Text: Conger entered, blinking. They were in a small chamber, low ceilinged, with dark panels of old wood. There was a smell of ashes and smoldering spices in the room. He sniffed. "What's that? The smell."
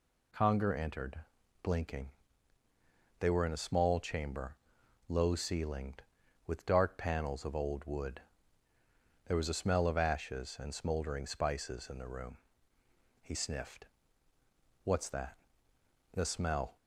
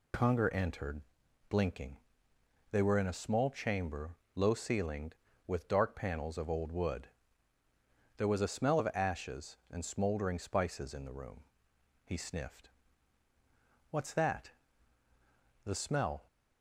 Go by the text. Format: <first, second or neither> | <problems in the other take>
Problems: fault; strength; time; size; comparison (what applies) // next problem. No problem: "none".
neither | none